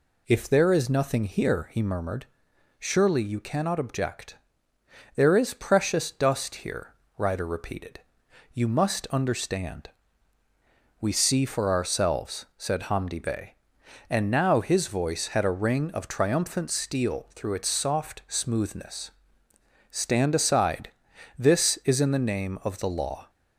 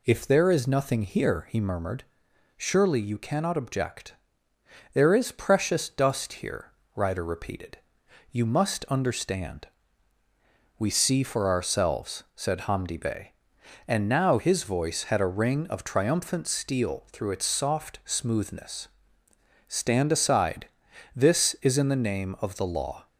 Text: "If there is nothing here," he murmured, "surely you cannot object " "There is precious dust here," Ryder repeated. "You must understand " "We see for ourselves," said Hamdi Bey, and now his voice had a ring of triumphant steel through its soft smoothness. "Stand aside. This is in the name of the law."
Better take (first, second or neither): neither